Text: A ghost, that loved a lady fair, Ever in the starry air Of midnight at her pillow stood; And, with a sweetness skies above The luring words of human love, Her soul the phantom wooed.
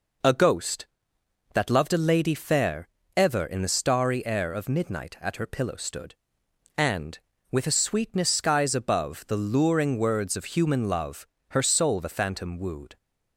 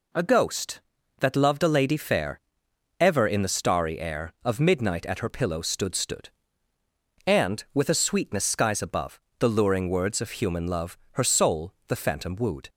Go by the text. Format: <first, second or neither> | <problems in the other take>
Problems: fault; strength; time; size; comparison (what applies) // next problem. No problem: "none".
first | says "stood" twice; at 5.9 s // pauses between "above" and "The"; slight; at 9.2 s; 0.16 s long // pauses between "soul" and "the"; slight; at 11.7 s; 0.16 s long